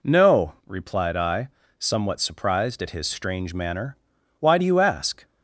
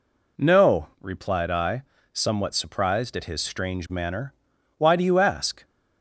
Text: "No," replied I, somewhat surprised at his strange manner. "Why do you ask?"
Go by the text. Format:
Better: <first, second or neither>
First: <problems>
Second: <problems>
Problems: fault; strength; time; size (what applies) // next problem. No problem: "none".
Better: neither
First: none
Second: none